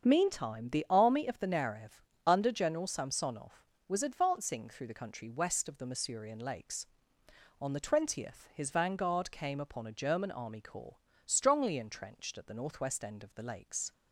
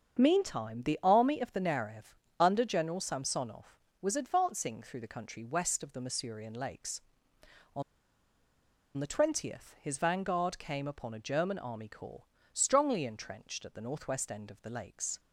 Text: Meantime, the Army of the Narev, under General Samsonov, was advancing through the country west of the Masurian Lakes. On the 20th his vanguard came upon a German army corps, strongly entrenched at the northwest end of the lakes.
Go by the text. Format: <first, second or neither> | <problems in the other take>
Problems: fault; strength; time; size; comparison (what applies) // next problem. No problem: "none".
first | starts louder than the rest; strong; until 1.2 s; 7 dB; strong in the first // pauses between "On" and "the"; at 7.8 s; 1.1 s long